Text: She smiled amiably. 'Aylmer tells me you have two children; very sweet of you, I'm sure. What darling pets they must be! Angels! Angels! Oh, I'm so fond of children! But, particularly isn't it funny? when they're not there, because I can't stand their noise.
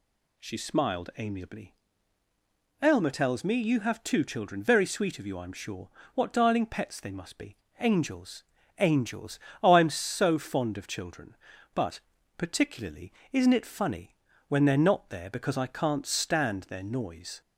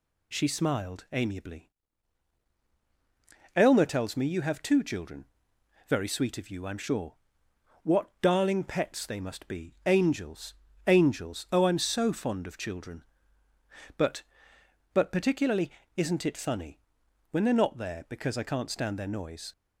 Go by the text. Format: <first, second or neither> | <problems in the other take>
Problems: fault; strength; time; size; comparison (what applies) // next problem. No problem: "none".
first | says "But" twice; at 14.9 s // pauses between "particularly" and "isn't"; slight; at 15.6 s; 0.28 s long; slight in the first